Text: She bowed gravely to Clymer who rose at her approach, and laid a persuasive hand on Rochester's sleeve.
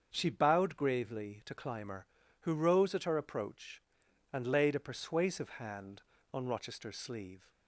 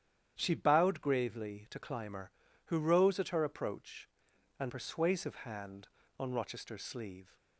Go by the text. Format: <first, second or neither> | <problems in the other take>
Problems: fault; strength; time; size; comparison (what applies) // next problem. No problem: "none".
first | starts louder than the rest; strong; until 1.3 s; 9.5 dB; also in the first // skips "laid a"; at 4.6 s